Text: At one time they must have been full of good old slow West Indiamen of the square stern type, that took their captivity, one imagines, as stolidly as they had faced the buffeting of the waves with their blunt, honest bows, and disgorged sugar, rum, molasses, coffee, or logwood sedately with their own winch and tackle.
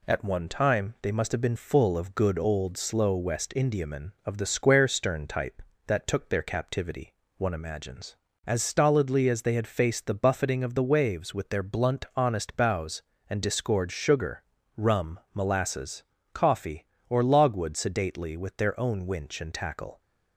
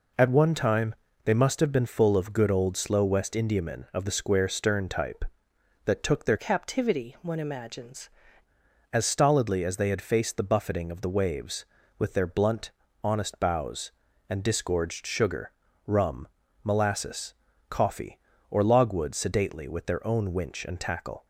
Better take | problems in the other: first | pauses between "time" and "they"; slight; at 0.9 s; 0.30 s long // changes voice from "captivity" to "imagines"; from 6.3 to 8.0 s; 1.7 s long

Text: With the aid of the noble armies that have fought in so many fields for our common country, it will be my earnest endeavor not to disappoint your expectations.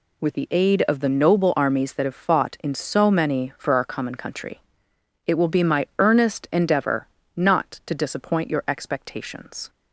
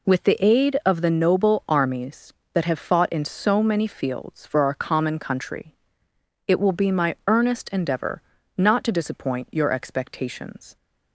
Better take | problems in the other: second | skips "fields"; at 3.5 s // pauses between "endeavor" and "not"; slight; at 7.0 s; 0.30 s long; slight in the second

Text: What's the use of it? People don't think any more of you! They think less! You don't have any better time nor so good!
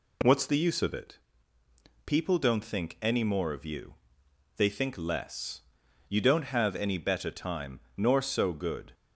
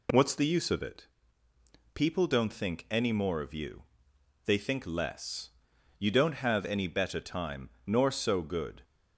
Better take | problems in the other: neither | pauses between "time" and "nor"; slight; the same in both

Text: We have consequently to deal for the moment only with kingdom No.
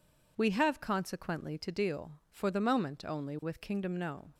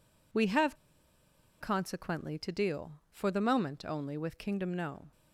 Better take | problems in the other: first | pauses between "have" and "consequently"; noticeable; at 0.7 s; 0.84 s long

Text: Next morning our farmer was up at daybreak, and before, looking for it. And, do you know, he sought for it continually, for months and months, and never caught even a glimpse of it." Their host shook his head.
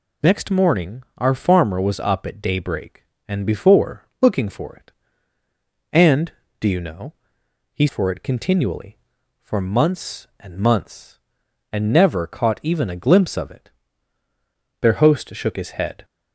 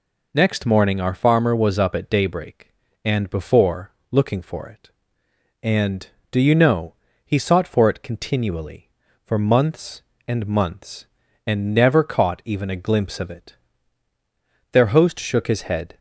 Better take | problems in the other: second | pauses between "morning" and "our"; slight; at 1.0 s; 0.16 s long // skips "sought"; at 7.8 s

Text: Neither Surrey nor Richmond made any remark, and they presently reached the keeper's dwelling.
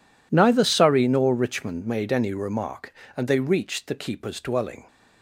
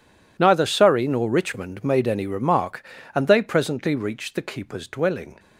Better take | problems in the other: second | skips "presently"; at 3.3 s

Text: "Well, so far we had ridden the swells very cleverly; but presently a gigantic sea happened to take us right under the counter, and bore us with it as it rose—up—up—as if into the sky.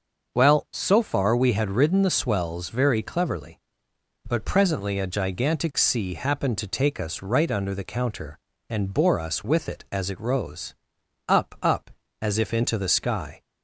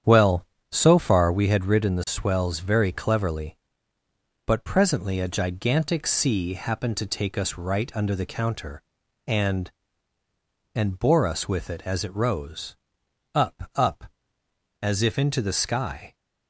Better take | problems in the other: first | starts louder than the rest; strong; until 1.3 s; 9 dB; also in the first // says "and" twice; at 10.7 s

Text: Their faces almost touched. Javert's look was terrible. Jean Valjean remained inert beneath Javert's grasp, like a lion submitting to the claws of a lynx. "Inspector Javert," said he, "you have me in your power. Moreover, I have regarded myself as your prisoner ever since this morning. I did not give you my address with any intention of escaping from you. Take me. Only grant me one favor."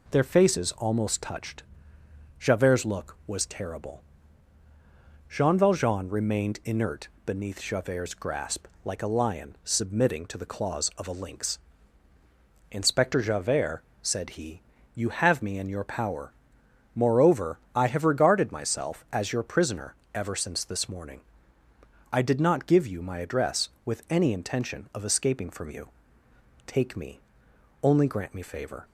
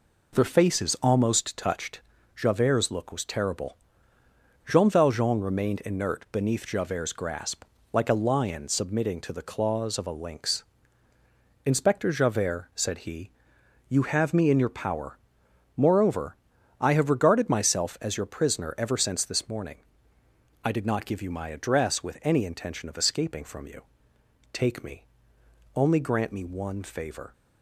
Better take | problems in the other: second | pauses between "inert" and "beneath"; slight; at 7.0 s; 0.16 s long // pauses between "prisoner" and "ever"; slight; at 19.9 s; 0.20 s long // skips "one"; at 28.4 s

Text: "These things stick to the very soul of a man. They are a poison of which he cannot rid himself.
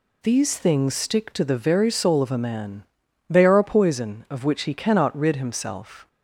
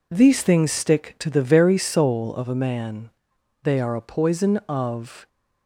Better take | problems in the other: first | stops before "which he cannot rid himself"; at 5.2 s

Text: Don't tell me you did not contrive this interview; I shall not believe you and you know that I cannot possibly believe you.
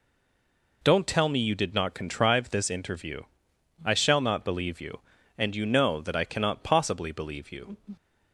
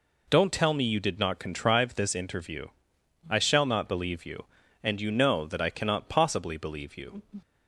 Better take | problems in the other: second | stays silent before the first word; slight; until 0.8 s; 0.8 s long

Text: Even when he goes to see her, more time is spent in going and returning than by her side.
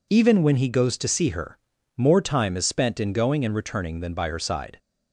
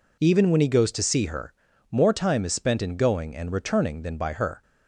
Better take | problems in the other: first | stops before "side"; at 4.6 s

